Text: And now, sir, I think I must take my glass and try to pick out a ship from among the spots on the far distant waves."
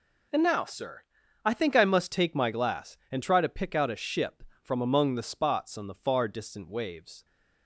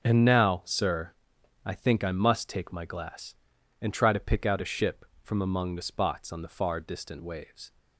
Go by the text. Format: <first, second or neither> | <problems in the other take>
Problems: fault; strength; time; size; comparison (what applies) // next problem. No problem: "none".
neither | none